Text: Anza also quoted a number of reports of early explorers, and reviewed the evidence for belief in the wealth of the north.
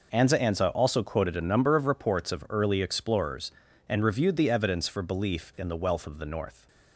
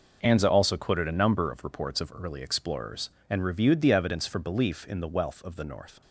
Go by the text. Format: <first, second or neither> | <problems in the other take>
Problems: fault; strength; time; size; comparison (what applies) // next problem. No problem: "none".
second | says "Anza" twice; at 0.3 s